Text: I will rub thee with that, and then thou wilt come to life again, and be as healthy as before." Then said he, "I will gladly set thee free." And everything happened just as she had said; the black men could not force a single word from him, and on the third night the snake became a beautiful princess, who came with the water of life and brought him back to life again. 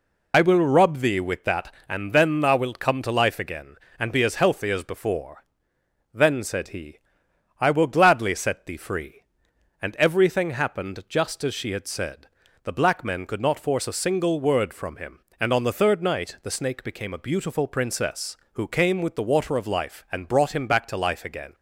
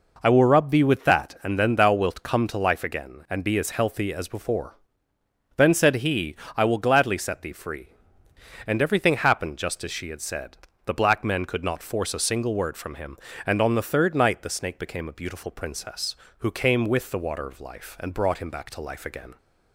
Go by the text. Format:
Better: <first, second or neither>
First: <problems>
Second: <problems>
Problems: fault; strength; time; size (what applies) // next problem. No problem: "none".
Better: second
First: loses the start of "I"; at 0.3 s; 40 ms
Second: none